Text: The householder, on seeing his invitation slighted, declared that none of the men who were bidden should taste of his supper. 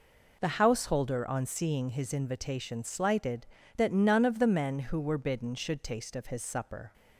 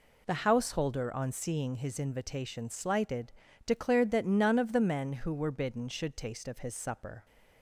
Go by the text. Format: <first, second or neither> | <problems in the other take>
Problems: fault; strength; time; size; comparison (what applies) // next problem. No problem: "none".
second | skips "declared"; at 3.6 s